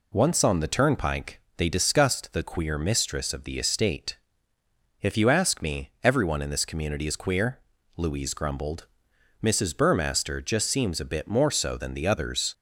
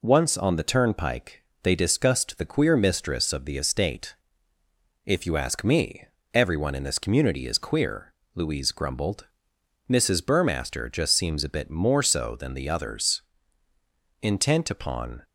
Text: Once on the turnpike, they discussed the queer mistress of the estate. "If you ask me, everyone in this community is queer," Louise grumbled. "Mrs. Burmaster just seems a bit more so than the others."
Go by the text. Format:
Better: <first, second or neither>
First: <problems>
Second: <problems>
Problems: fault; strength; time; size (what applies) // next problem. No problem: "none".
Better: first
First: none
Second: goes on to say "Intent upon"; noticeable; from 14.2 s on; 0.98 s long